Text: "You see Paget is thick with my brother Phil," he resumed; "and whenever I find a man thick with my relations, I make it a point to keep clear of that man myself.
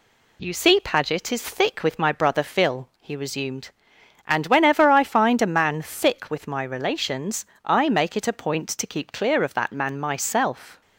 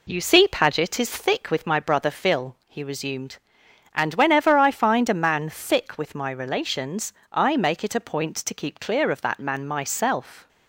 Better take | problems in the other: first | starts louder than the rest; slight; until 1.4 s; 3 dB

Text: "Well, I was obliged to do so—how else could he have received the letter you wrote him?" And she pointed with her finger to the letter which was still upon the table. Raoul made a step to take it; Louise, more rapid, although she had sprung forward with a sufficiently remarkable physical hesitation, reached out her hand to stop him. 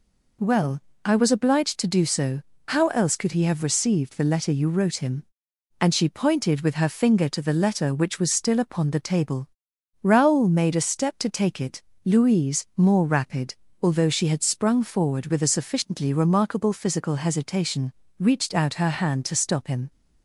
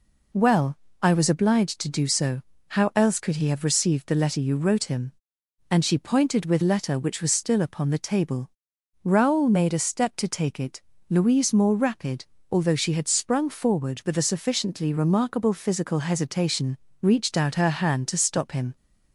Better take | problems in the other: first | skips "her finger to the"; at 6.6 s

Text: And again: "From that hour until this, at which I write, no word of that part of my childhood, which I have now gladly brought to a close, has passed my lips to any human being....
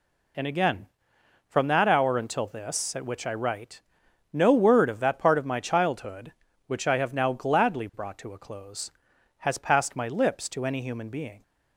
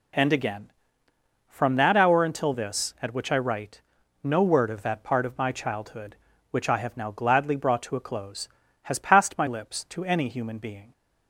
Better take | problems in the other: neither | none

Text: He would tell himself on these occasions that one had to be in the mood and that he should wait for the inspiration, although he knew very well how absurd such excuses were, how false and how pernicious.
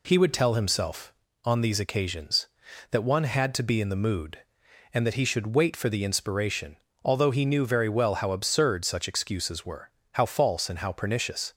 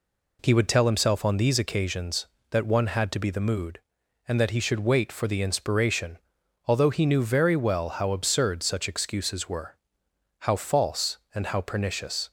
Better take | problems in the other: first | skips "in"; at 3.3 s

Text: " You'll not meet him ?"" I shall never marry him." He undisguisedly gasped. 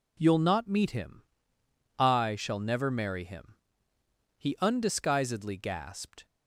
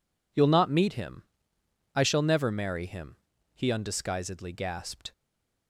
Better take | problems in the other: first | stays silent after the last word; slight; from 5.1 s on; 0.5 s long

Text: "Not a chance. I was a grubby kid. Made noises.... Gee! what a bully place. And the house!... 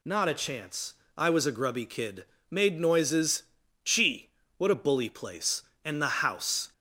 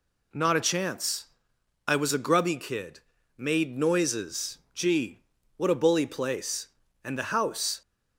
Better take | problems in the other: neither | none

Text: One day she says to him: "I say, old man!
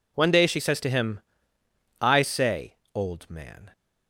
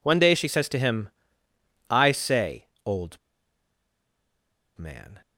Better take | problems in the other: first | pauses between "old" and "man"; strong; at 3.1 s; 1.6 s long

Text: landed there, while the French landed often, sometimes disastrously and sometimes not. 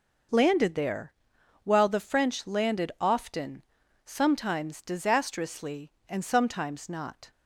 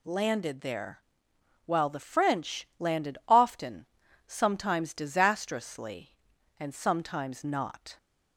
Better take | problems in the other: neither | none

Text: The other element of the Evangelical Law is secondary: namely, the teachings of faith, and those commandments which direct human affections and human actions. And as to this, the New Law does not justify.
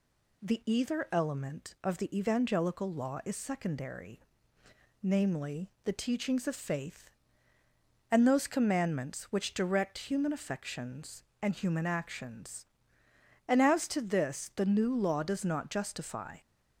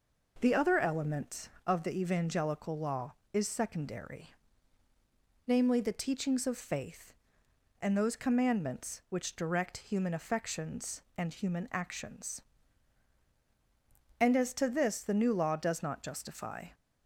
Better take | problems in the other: second | says "either" for "other"; at 0.6 s

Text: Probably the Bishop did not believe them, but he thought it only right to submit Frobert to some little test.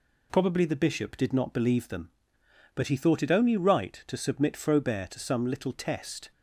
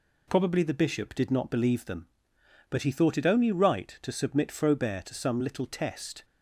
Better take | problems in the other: neither | none

